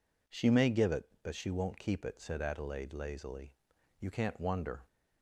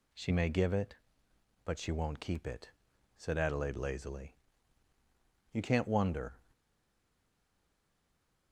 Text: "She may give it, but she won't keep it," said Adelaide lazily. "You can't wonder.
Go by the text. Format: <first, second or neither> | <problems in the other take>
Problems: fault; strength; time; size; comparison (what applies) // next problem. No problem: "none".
first | stays silent after the last word; noticeable; from 6.5 s on; 2.0 s long